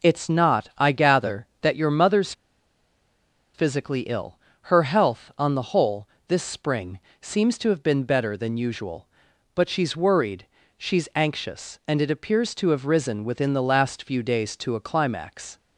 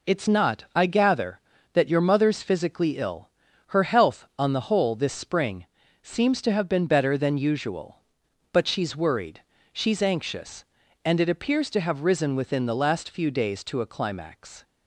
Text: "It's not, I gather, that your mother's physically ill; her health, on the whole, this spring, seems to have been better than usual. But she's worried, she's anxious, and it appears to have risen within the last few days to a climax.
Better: second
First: pauses between "mother's" and "physically"; at 2.3 s; 1.2 s long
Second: none

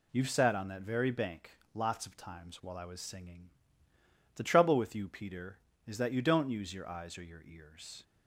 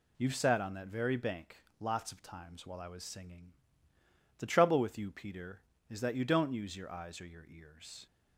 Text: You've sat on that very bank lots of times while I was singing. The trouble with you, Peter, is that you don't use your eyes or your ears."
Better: neither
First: pauses between "bank" and "lots"; slight; at 1.5 s; 0.24 s long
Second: pauses between "bank" and "lots"; slight; at 1.5 s; 0.24 s long

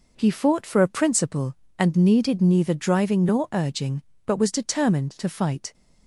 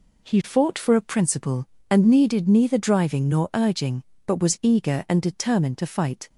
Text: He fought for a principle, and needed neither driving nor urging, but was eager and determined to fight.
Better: second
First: skips "eager and"; at 4.5 s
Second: none

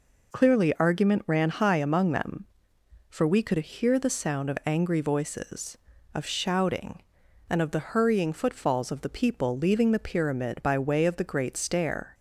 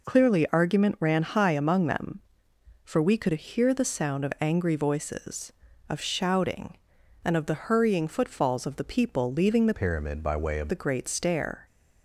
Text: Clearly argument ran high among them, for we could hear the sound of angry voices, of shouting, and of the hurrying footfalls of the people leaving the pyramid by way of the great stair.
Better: first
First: none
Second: changes voice from "pyramid" to "of"; from 9.7 to 10.7 s; 1.0 s long

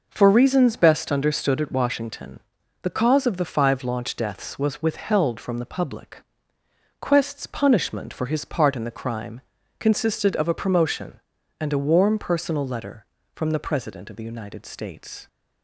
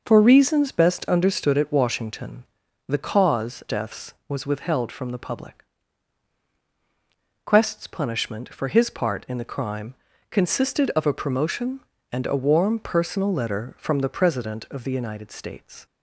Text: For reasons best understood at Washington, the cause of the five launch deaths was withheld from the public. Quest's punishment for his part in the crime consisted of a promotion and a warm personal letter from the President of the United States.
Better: first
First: pauses between "crime" and "consisted"; at 9.3 s; 0.40 s long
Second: skips "of the five launch"; at 3.6 s // pauses between "crime" and "consisted"; at 9.9 s; 0.38 s long

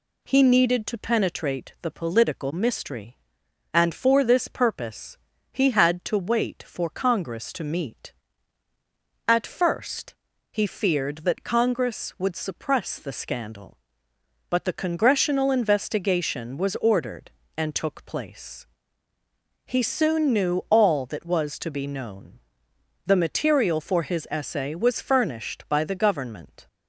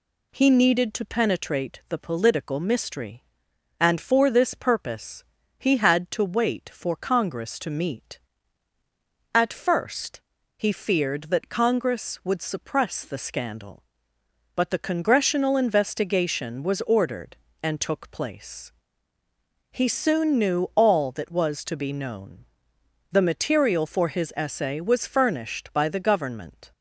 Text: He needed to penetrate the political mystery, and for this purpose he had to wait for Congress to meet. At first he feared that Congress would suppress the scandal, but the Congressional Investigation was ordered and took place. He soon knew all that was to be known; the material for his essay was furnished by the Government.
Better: neither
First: pauses between "purpose" and "he"; slight; at 5.1 s; 0.34 s long // pauses between "first" and "he"; slight; at 10.1 s; 0.36 s long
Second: pauses between "purpose" and "he"; slight; at 5.2 s; 0.34 s long // pauses between "first" and "he"; slight; at 10.2 s; 0.35 s long

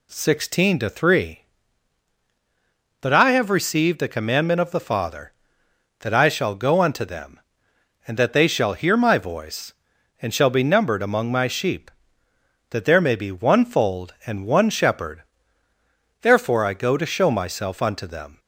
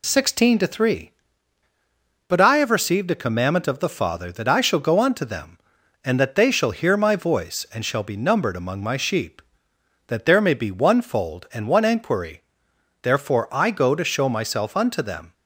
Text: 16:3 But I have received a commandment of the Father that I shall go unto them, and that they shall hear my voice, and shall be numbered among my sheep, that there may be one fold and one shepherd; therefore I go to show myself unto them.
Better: first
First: none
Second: says "enquiry" for "shepherd"; at 11.8 s

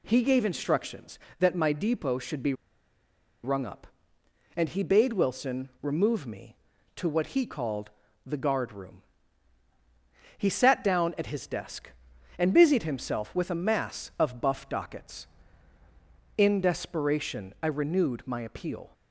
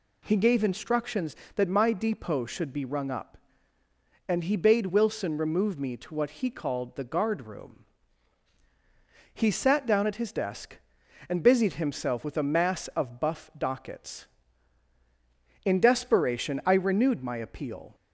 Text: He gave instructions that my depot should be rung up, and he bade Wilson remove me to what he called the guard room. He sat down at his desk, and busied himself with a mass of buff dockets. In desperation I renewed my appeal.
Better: second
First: pauses between "be" and "rung"; noticeable; at 2.5 s; 0.90 s long // pauses between "called" and "the"; at 7.8 s; 0.38 s long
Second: none

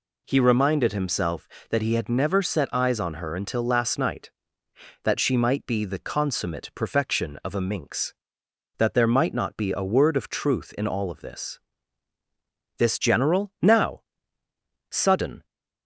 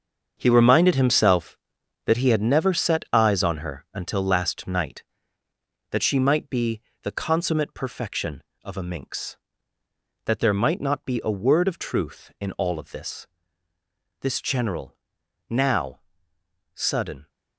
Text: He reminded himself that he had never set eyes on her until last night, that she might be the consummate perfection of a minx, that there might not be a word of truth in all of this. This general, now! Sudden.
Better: first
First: none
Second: gets quieter; strong; throughout; 10.5 dB // pauses between "be" and "the"; slight; at 6.8 s; 0.22 s long

